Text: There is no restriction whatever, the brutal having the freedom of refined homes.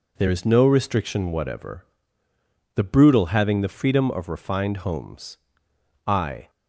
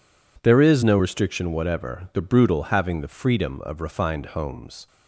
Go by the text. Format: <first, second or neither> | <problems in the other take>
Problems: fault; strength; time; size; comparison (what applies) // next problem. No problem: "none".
second | goes on to say "I"; slight; from 6.0 s on; 0.44 s long